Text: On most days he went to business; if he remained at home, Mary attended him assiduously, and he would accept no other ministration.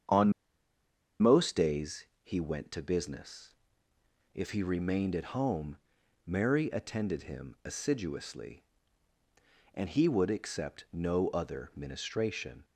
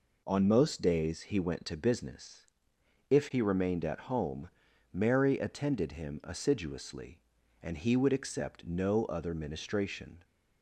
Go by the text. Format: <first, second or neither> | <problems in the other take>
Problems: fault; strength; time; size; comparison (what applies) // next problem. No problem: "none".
second | starts louder than the rest; strong; until 1.9 s; 8 dB // pauses between "On" and "most"; noticeable; at 0.3 s; 0.90 s long // pauses between "days" and "he"; slight; at 2.0 s; 0.18 s long